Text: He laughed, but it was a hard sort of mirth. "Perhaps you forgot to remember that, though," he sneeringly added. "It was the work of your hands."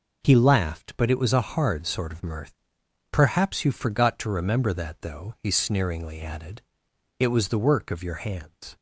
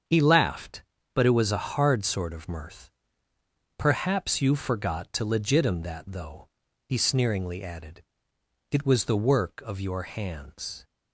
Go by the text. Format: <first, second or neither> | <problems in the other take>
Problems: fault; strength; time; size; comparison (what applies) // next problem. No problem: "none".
first | starts louder than the rest; strong; until 1.4 s; 7.5 dB // says "legitim" for "remember"; at 5.2 s